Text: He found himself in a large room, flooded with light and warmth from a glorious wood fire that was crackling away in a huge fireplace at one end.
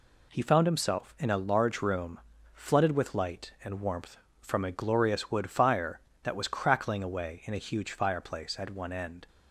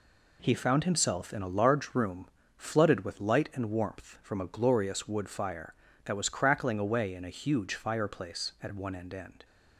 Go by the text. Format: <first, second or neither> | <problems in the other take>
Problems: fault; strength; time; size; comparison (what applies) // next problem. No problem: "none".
first | says "end" twice; at 9.1 s